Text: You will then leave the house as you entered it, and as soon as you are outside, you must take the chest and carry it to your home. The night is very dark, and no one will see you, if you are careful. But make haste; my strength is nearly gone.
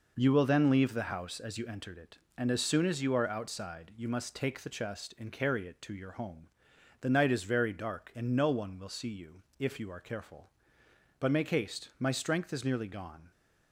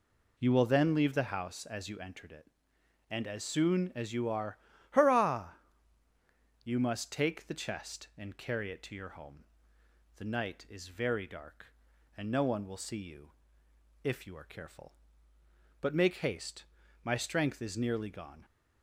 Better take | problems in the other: first | says "hurrah" for "outside"; at 4.9 s

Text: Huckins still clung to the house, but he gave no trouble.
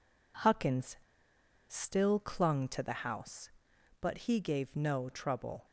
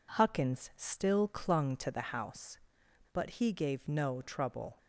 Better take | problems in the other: second | pauses between "Huckins" and "still"; noticeable; at 0.9 s; 0.71 s long

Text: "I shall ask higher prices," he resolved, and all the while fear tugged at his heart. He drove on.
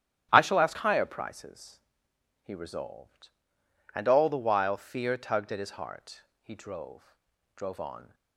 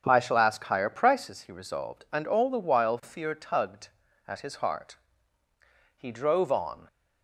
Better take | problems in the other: second | starts louder than the rest; strong; until 1.3 s; 12 dB; strong in the second // says "drove" twice; at 7.5 s

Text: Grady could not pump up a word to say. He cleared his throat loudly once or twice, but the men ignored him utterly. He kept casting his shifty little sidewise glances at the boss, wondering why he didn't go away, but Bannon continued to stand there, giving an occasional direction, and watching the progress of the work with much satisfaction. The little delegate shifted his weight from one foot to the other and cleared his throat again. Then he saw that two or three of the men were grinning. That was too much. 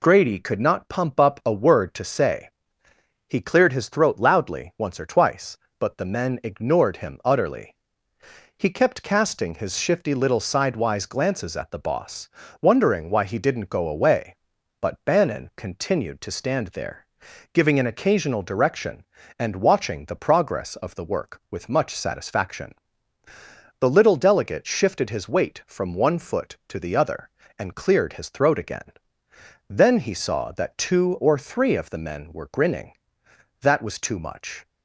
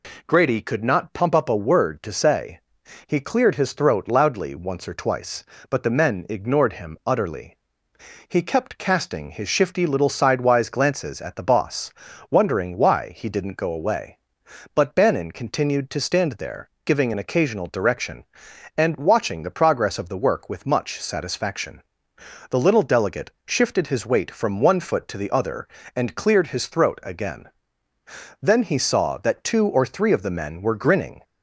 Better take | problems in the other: first | pauses between "delegate" and "shifted"; slight; at 23.2 s; 0.16 s long // stops before "That was too much"; at 31.2 s

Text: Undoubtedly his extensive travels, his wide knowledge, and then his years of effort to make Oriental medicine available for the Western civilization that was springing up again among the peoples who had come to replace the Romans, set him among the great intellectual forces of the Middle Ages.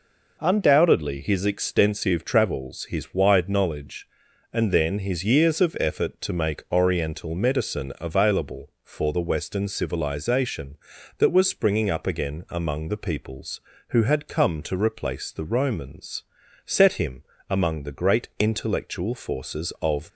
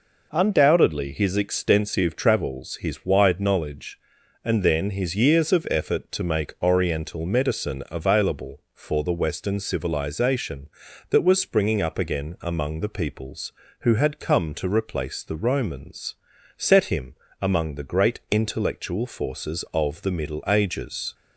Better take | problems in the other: second | pauses between "him" and "among"; slight; at 17.2 s; 0.26 s long; slight in the second // stops before "the Middle Ages"; at 20.1 s

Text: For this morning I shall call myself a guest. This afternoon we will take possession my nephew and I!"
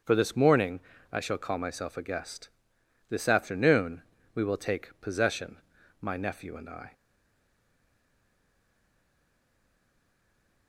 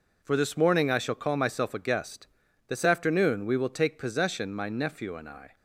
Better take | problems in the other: second | starts louder than the rest; until 1.3 s; 6.5 dB // pauses between "morning" and "I"; slight; at 0.7 s; 0.34 s long // pauses between "afternoon" and "we"; slight; at 4.0 s; 0.32 s long // pauses between "possession" and "my"; at 5.5 s; 0.44 s long // stays silent after the last word; strong; from 6.9 s on; 3.7 s long

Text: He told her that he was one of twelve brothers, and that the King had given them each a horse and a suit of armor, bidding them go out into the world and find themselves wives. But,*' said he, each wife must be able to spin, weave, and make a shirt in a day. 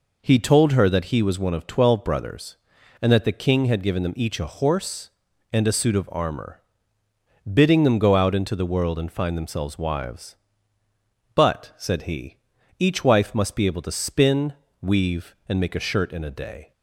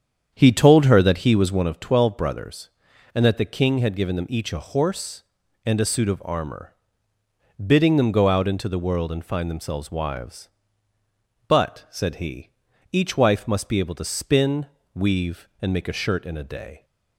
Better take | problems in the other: first | starts louder than the rest; strong; until 1.8 s; 8 dB

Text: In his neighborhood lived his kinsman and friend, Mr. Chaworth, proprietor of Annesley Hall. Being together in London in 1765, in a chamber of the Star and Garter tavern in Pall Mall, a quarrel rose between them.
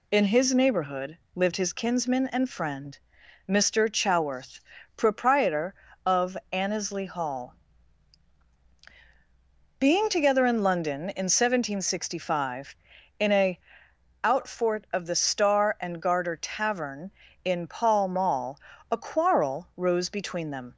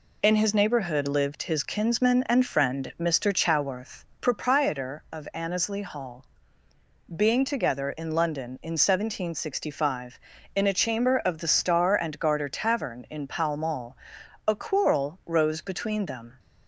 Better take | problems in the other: second | pauses between "neighborhood" and "lived"; slight; at 1.1 s; 0.18 s long // says "outfort" for "chamber"; at 14.2 s

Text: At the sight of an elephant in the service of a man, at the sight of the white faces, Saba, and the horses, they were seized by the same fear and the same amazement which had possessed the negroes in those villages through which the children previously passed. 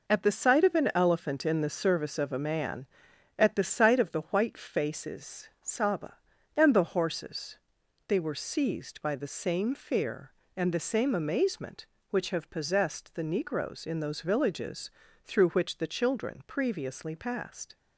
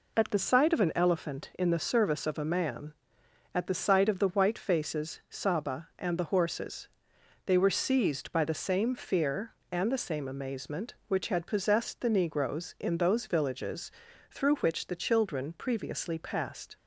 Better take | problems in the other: second | says "have" for "had"; at 12.3 s // pauses between "villages" and "through"; slight; at 14.9 s; 0.34 s long; also in the second

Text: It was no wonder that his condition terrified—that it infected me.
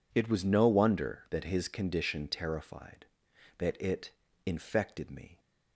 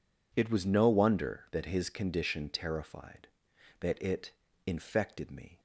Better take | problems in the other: neither | pauses between "it" and "infected"; slight; the same in both

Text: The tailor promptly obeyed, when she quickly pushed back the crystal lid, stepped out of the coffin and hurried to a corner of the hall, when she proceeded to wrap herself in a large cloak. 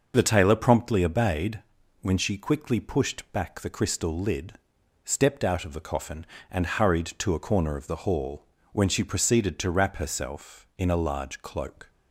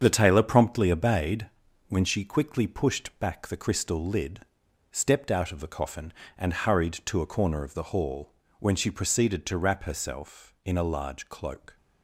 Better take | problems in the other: first | gets quieter; strong; throughout; 8 dB

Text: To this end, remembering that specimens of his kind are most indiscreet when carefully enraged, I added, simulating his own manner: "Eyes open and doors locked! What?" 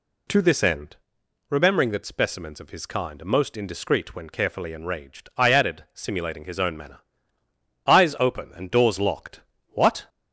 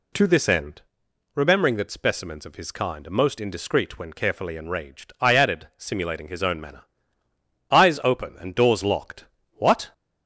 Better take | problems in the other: neither | none

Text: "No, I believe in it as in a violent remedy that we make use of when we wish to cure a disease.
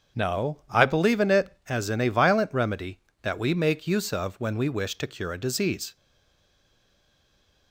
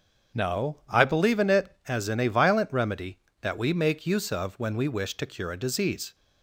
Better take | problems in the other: second | starts louder than the rest; until 1.2 s; 7 dB; also in the second // stays silent after the last word; noticeable; from 5.9 s on; 1.8 s long

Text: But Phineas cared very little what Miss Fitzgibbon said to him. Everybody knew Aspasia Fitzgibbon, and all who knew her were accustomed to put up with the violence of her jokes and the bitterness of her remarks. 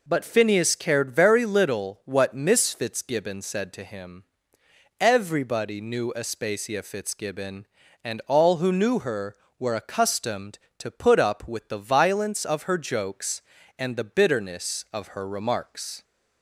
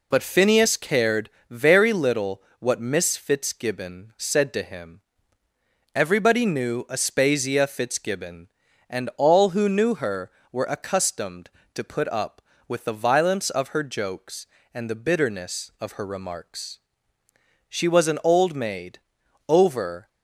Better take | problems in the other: first | pauses between "cared" and "very"; slight; at 1.2 s; 0.20 s long // pauses between "little" and "what"; slight; at 2.4 s; 0.18 s long // goes on to say "She was an old maid over"; strong; from 17.6 s on; 2.4 s long

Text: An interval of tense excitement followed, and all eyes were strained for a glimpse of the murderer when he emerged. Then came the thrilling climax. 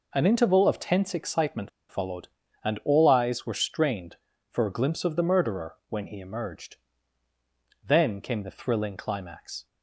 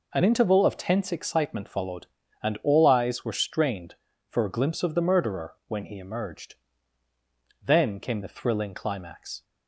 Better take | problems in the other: second | pauses between "excitement" and "followed"; slight; at 1.6 s; 0.19 s long

